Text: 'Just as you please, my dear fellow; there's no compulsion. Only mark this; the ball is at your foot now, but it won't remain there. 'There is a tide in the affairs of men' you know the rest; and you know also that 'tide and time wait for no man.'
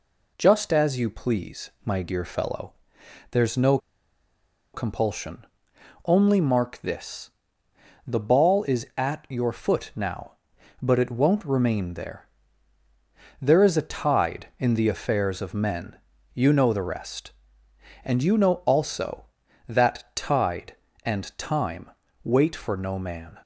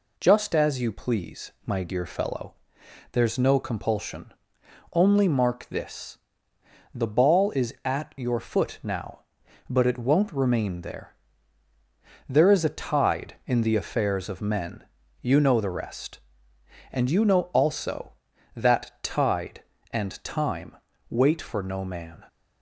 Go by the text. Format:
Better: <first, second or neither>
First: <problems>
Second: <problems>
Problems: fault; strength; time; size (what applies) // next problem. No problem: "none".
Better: second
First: pauses between "no" and "compulsion"; noticeable; at 3.7 s; 0.96 s long // pauses between "men" and "you"; slight; at 15.9 s; 0.36 s long // pauses between "time" and "wait"; slight; at 21.8 s; 0.34 s long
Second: pauses between "men" and "you"; slight; at 14.8 s; 0.36 s long // pauses between "time" and "wait"; slight; at 20.7 s; 0.34 s long